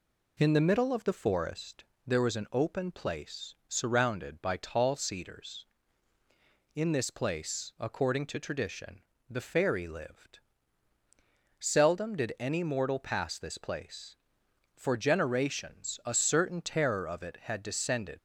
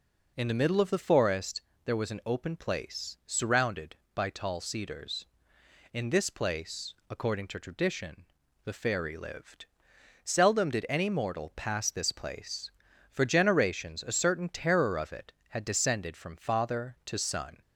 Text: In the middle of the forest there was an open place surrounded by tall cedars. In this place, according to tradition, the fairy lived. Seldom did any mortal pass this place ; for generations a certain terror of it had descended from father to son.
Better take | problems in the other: second | pauses between "forest" and "there"; slight; at 1.8 s; 0.24 s long; slight in the second // stops before "from father to son"; at 18.1 s

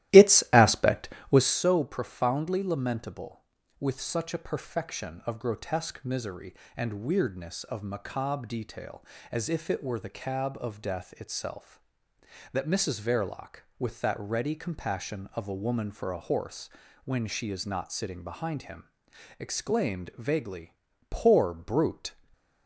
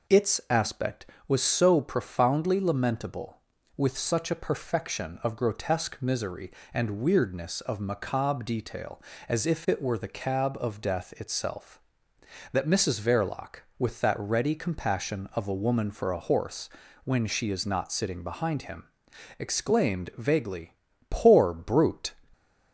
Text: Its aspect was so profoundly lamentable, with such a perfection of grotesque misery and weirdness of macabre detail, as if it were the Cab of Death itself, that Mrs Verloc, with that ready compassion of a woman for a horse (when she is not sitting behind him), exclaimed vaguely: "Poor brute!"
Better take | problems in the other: second | starts louder than the rest; strong; until 1.5 s; 15 dB // stays silent after the last word; slight; from 22.0 s on; 0.6 s long

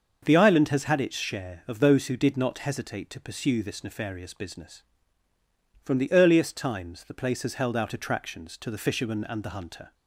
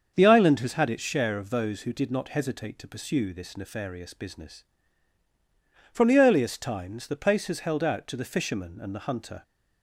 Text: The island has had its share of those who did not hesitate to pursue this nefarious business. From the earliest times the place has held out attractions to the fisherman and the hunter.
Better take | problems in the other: first | starts louder than the rest; until 1.1 s; 7 dB; also in the first // skips "attractions"; at 8.0 s

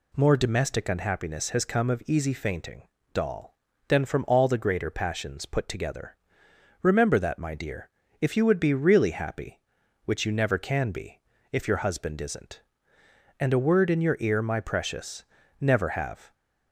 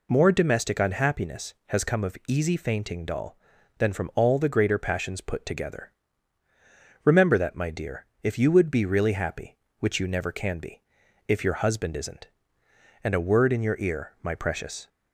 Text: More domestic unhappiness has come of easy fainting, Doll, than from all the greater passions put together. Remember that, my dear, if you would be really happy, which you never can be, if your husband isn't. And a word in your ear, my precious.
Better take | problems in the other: second | goes on to say "Never have"; noticeable; from 15.5 s on; 0.74 s long

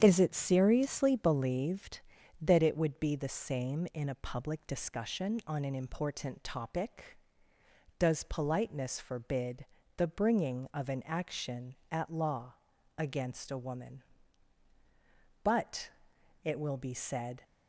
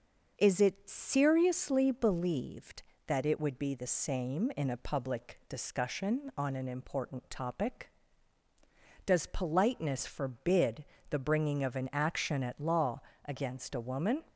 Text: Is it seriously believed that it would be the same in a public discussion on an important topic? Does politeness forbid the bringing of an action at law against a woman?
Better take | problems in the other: second | starts louder than the rest; strong; until 1.0 s; 8.5 dB // pauses between "forbid" and "the"; slight; at 9.6 s; 0.30 s long; slight in the second // pauses between "law" and "against"; at 12.5 s; 0.42 s long; slight in the second // goes on to say "But it will be said"; strong; from 15.4 s on; 2.0 s long

